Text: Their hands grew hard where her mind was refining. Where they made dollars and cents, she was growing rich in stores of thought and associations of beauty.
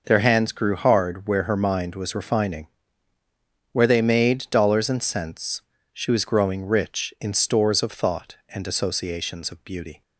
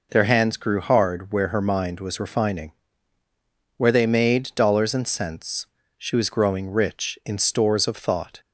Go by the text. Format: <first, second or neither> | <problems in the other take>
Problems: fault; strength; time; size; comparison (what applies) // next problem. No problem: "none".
first | stops before "and associations of beauty"; at 8.4 s